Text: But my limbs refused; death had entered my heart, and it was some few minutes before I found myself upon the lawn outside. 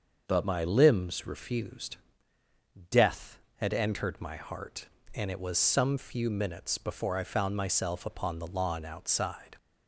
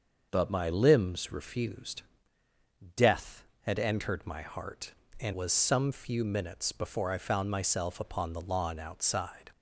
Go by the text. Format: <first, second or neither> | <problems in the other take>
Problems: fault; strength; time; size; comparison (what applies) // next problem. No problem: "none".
first | starts louder than the rest; until 1.3 s; 6 dB; also in the first // skips "it"; at 5.3 s